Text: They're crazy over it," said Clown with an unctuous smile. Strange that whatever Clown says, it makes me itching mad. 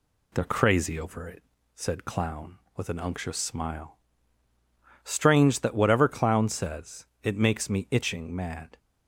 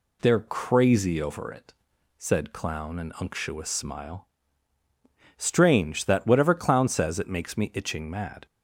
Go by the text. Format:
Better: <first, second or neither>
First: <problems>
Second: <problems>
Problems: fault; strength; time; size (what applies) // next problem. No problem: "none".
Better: first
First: none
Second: skips "with"; at 2.9 s